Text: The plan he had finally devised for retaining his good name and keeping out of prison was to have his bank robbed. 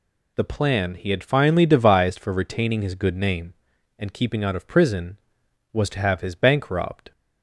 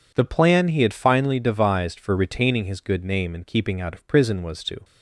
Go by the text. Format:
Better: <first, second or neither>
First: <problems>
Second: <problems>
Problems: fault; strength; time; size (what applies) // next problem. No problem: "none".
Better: first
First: none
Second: stops before "have his bank robbed"; at 4.8 s